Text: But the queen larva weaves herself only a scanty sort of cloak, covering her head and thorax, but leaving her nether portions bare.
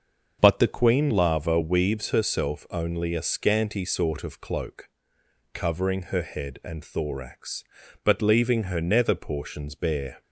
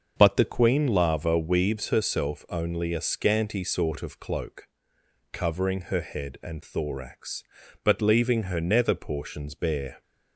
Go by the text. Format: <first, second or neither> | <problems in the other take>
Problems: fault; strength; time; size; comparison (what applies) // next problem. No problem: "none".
neither | starts louder than the rest; the same in both